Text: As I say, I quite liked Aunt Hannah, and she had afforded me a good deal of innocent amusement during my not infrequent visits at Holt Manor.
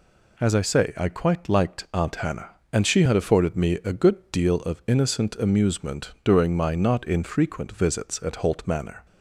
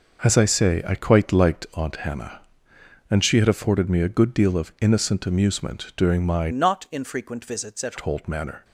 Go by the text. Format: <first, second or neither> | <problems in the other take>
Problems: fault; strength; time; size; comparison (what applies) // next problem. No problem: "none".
first | changes voice from "not" to "at"; from 6.5 to 7.9 s; 1.4 s long